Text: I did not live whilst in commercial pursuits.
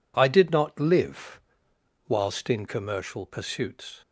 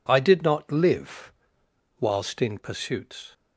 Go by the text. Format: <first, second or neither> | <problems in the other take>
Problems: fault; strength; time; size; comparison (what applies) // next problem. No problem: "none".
first | pauses between "live" and "whilst"; noticeable; at 1.3 s; 0.66 s long; noticeable in the first // skips "commercial"; at 2.5 s